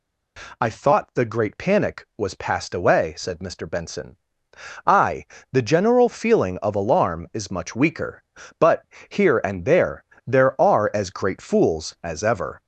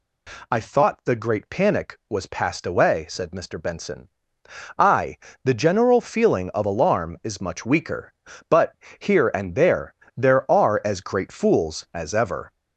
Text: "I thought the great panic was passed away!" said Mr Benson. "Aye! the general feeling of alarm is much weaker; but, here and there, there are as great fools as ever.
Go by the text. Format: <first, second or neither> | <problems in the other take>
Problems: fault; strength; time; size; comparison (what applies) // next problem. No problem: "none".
neither | none